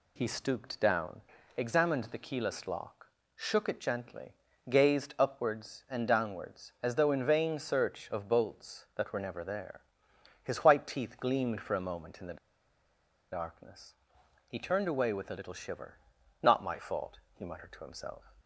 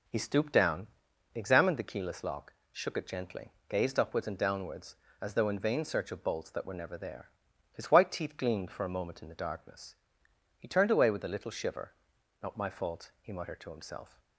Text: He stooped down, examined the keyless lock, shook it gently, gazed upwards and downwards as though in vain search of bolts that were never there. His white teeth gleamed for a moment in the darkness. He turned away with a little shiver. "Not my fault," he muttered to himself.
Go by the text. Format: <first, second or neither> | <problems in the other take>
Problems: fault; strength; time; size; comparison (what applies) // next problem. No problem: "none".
second | pauses between "the" and "darkness"; noticeable; at 12.3 s; 0.95 s long